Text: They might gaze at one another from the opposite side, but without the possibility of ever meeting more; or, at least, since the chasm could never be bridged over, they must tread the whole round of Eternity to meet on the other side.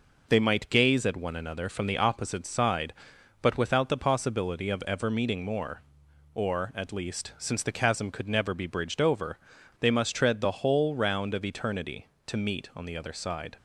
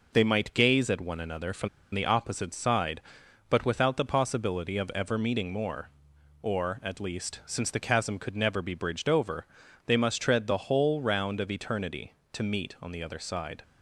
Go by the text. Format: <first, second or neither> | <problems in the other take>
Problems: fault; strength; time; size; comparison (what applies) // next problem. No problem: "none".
first | pauses between "from" and "the"; slight; at 1.6 s; 0.25 s long